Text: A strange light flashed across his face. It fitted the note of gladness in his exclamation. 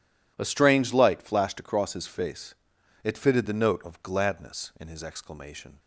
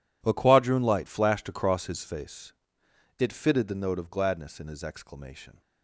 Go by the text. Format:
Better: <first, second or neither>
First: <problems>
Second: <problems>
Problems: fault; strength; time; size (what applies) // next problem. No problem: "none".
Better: first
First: none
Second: says "quadroon" for "strange"; at 0.3 s